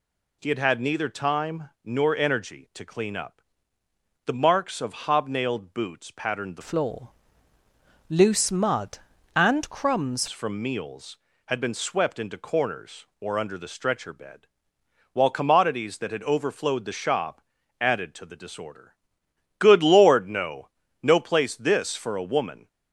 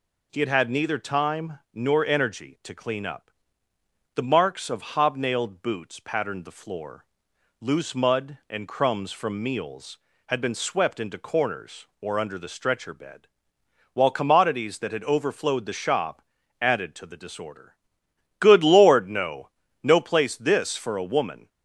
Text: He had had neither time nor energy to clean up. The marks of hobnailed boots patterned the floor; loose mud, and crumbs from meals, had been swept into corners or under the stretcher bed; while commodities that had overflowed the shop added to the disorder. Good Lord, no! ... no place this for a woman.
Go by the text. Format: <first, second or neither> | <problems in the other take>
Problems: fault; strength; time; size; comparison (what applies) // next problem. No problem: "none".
second | changes voice from "floor" to "crumbs"; from 6.6 to 10.2 s; 3.6 s long // pauses between "shop" and "added"; at 17.3 s; 0.40 s long; also in the second